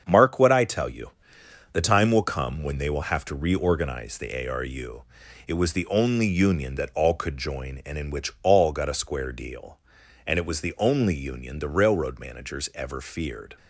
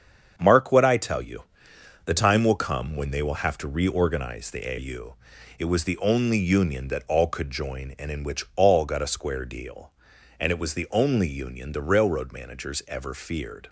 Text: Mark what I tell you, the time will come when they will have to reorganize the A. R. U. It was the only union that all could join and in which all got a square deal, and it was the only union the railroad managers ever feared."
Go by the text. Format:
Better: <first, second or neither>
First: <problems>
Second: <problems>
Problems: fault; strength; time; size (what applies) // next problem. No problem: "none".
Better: first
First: starts louder than the rest; strong; until 1.0 s; 7 dB // pauses between "U" and "It"; at 5.0 s; 0.44 s long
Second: starts louder than the rest; strong; until 1.3 s; 7 dB // skips "R"; at 4.7 s // pauses between "U" and "It"; at 5.1 s; 0.44 s long